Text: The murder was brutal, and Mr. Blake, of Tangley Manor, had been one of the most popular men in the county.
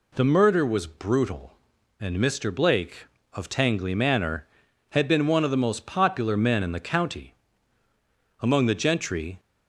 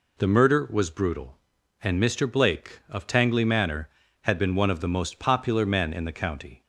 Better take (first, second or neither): second